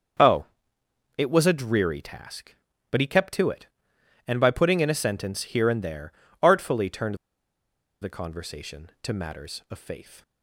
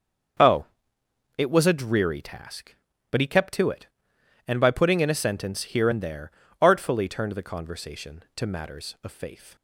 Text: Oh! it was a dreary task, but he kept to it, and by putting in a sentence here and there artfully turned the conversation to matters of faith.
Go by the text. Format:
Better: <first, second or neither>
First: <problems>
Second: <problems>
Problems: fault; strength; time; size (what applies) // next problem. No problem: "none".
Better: second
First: starts louder than the rest; until 1.9 s; 6.5 dB // pauses between "there" and "artfully"; slight; at 6.1 s; 0.30 s long // pauses between "turned" and "the"; noticeable; at 7.1 s; 0.85 s long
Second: starts louder than the rest; until 2.1 s; 6.5 dB // pauses between "there" and "artfully"; slight; at 6.3 s; 0.30 s long